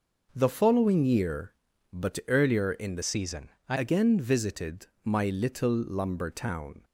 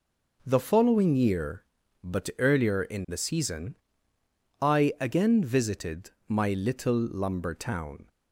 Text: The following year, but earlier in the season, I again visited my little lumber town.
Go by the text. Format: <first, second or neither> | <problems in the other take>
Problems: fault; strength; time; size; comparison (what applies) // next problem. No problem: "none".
second | changes voice from "season" to "I"; from 3.0 to 3.7 s; 0.7 s long // pauses between "visited" and "my"; slight; at 4.8 s; 0.18 s long; slight in the second